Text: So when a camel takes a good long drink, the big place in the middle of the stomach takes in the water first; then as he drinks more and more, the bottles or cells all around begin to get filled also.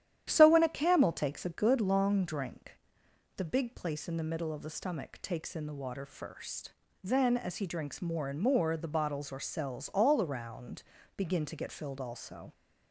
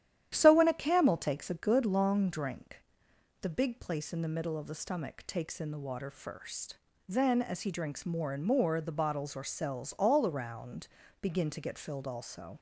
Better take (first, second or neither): neither